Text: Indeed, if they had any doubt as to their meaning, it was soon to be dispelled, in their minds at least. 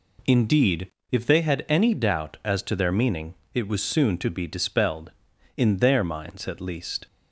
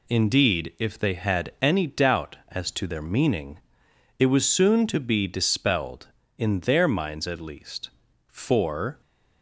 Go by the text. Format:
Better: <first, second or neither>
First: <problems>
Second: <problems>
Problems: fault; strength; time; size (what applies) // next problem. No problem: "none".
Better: first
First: none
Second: goes on to say "For"; noticeable; from 8.2 s on; 0.72 s long